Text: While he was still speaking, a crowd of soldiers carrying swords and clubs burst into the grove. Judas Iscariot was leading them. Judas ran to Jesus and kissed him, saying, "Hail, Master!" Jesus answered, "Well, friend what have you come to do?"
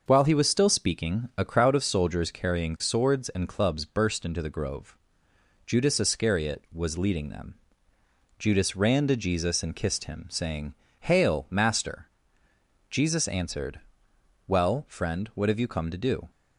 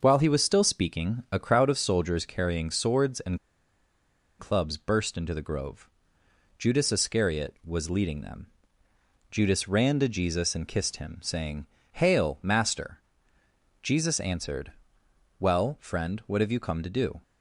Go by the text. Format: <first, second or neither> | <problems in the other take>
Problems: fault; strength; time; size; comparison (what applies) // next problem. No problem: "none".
first | starts louder than the rest; until 1.0 s; 6.5 dB; also in the first // pauses between "and" and "clubs"; at 3.3 s; 1.0 s long